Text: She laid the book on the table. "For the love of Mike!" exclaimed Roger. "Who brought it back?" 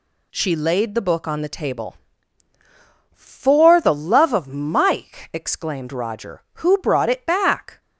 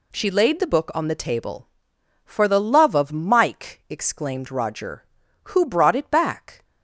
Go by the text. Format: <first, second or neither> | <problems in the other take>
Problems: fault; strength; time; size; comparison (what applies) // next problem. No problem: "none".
neither | none